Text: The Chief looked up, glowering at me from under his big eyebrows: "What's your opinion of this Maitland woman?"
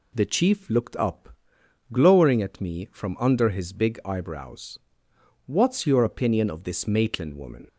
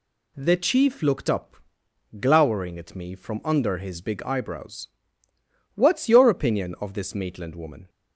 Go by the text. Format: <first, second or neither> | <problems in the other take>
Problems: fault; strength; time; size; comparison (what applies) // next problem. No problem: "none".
neither | none